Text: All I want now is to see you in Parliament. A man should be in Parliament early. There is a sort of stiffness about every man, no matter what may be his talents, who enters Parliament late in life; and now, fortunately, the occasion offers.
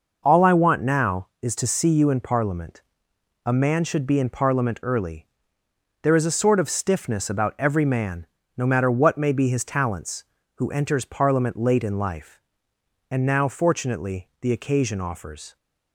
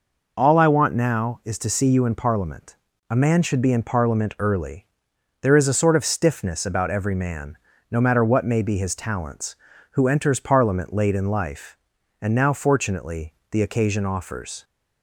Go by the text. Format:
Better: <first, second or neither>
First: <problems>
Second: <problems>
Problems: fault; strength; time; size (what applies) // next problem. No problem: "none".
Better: neither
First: none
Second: none